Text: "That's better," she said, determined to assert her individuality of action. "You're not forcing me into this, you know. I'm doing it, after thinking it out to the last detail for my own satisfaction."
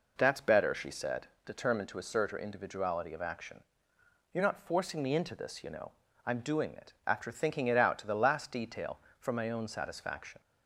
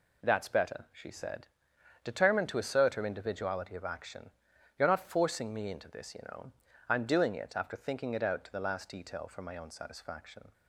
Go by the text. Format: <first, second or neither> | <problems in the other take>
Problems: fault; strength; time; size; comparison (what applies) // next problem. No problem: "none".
neither | none